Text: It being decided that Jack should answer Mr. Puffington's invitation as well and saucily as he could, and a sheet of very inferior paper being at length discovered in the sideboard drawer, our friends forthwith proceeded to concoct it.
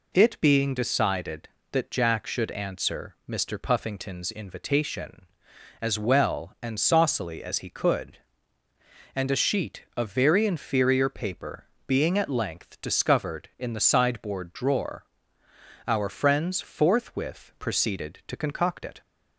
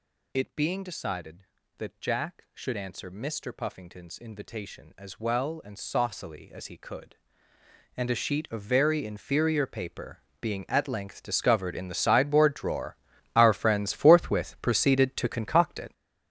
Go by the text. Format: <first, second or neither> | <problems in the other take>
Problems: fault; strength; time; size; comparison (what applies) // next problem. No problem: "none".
first | gets louder; strong; throughout; 12 dB // pauses between "paper" and "being"; slight; at 10.1 s; 0.24 s long; slight in the first